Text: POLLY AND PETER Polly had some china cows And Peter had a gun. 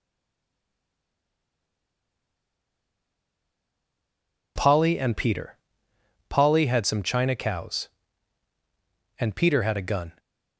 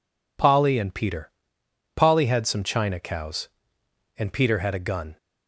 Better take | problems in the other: second | stays silent before the first word; strong; until 4.5 s; 4.5 s long // pauses between "PETER" and "Polly"; noticeable; at 5.5 s; 0.76 s long; noticeable in the second

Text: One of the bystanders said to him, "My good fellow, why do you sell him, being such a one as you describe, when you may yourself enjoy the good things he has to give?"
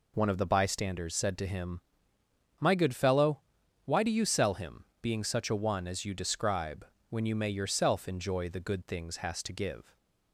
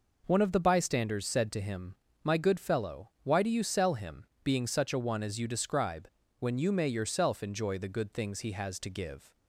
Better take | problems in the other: second | skips "he"; at 9.1 s

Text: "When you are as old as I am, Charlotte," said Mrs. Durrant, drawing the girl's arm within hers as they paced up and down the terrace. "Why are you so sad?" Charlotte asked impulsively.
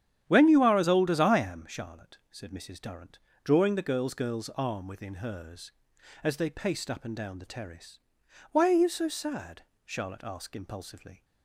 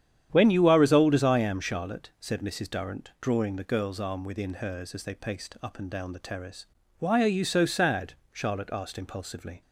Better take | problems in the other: second | starts louder than the rest; strong; until 1.2 s; 10 dB; strong in the second // says "girl's" twice; at 4.1 s

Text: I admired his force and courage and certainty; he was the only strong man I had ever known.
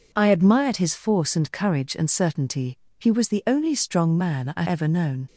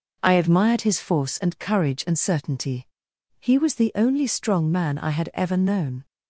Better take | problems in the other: second | skips "had"; at 4.6 s

